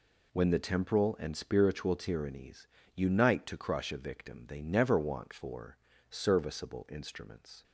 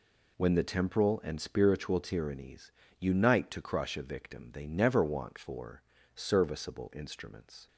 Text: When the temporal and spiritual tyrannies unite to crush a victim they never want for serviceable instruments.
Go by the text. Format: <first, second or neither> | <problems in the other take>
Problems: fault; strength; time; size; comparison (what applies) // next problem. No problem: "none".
neither | pauses between "tyrannies" and "unite"; slight; the same in both // pauses between "for" and "serviceable"; slight; the same in both